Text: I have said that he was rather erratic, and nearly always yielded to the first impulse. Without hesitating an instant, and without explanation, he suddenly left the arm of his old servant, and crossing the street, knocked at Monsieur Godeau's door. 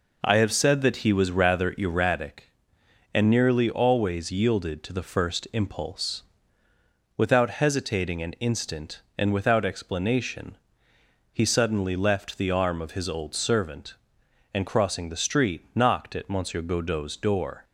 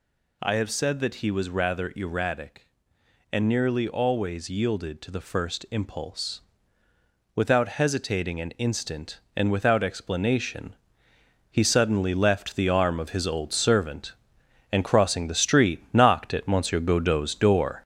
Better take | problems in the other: first | gets louder; noticeable; throughout; 5 dB

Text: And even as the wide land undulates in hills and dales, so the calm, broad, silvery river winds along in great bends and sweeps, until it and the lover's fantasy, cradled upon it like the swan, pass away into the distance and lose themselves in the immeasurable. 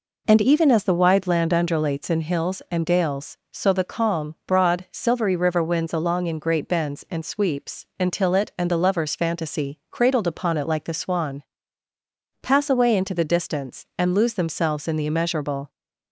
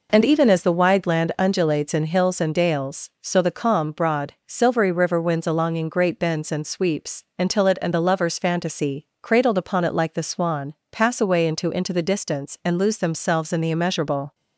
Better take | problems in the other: first | says "into" twice; at 11.7 s

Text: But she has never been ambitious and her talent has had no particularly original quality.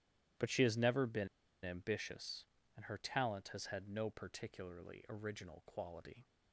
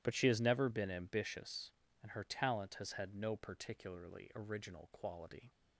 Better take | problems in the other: second | starts louder than the rest; strong; until 1.7 s; 12.5 dB; strong in the second // pauses between "been" and "ambitious"; at 1.2 s; 0.37 s long

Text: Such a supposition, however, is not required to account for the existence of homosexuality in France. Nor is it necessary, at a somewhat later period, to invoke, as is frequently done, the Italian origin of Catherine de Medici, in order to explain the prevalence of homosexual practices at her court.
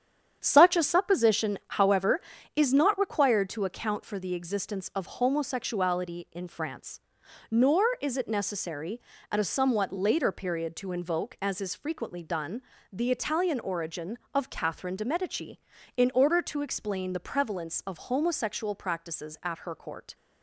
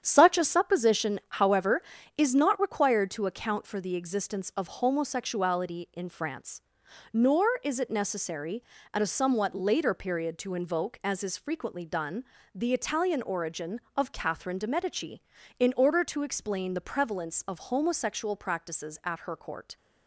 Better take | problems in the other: neither | starts louder than the rest; strong; the same in both

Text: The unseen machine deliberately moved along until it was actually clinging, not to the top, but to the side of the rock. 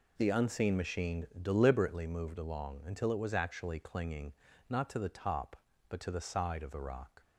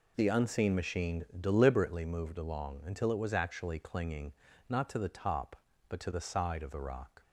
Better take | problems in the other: neither | pauses between "machine" and "deliberately"; slight; the same in both

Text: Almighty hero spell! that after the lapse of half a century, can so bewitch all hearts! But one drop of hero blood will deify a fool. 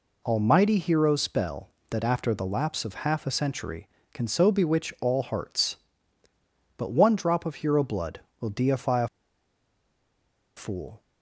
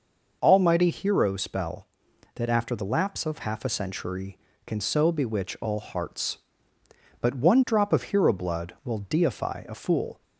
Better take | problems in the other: second | pauses between "a" and "fool"; strong; at 9.0 s; 1.4 s long

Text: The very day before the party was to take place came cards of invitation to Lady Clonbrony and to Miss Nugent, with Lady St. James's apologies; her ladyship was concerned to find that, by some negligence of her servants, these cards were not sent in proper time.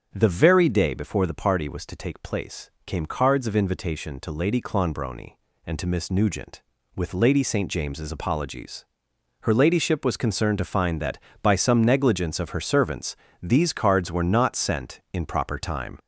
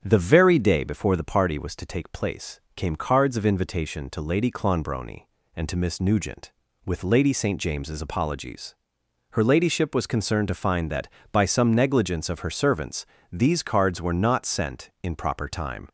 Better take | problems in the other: second | gets louder; throughout; 3.5 dB // starts louder than the rest; strong; until 1.1 s; 7.5 dB; strong in the second // pauses between "place" and "came"; slight; at 2.6 s; 0.16 s long; slight in the second

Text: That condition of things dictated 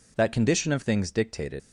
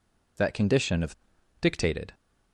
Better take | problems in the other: first | skips "things"; at 1.3 s

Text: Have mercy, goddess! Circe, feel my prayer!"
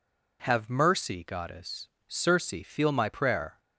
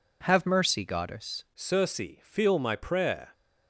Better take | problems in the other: first | changes voice at "Circe"; from 1.5 s on; 1.8 s long

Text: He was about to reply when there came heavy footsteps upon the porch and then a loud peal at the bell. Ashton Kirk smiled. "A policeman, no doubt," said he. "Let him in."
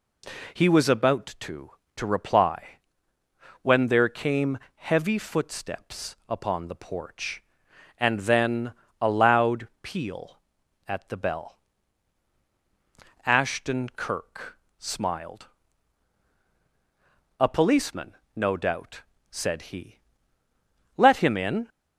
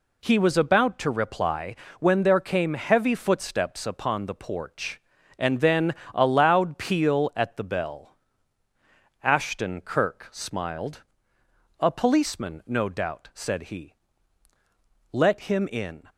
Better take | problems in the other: second | says "to" twice; at 1.9 s // pauses between "reply" and "when"; noticeable; at 2.7 s; 0.84 s long; slight in the second // pauses between "came" and "heavy"; slight; at 4.5 s; 0.16 s long // pauses between "then" and "a"; slight; at 8.7 s; 0.28 s long; slight in the second // pauses between "Kirk" and "smiled"; slight; at 14.5 s; 0.20 s long

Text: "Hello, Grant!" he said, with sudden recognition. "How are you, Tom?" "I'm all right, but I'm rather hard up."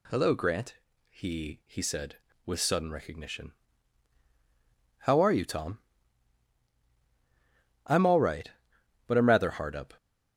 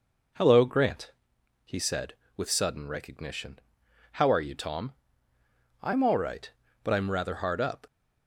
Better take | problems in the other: second | says "he" twice; at 1.6 s

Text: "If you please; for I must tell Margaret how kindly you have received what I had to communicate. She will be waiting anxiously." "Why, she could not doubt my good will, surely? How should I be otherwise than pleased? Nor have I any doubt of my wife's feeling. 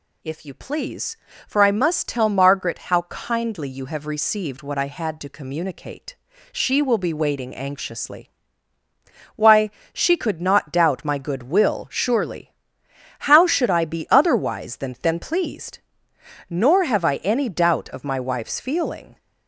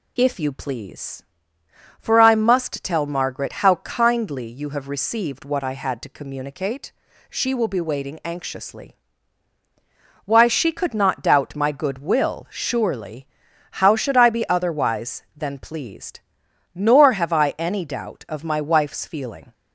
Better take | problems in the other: second | says "than" twice; at 15.0 s

